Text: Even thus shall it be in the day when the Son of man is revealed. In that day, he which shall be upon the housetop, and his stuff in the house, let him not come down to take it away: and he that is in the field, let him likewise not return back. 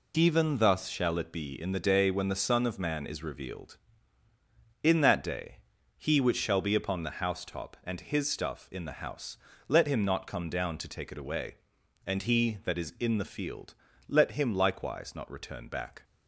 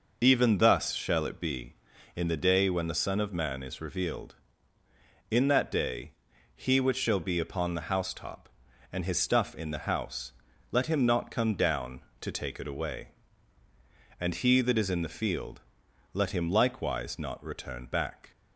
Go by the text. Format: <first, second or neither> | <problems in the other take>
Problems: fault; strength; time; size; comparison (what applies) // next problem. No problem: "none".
neither | none